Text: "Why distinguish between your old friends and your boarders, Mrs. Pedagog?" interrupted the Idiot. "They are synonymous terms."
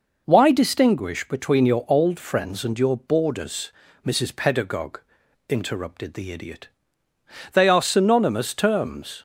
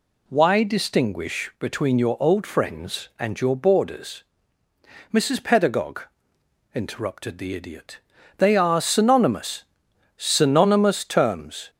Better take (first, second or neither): first